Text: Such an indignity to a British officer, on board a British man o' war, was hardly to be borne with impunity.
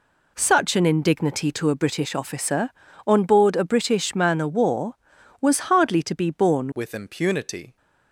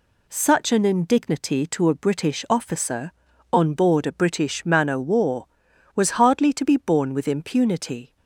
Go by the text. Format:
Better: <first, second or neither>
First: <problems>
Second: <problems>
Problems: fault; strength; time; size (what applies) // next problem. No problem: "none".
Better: second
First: changes voice at "with"; from 6.7 s on; 1.0 s long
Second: none